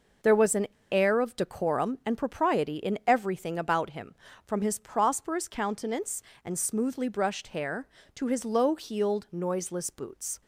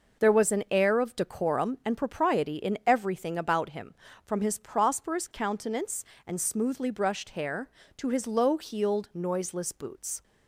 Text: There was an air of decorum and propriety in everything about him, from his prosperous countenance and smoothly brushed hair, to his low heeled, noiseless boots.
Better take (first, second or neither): second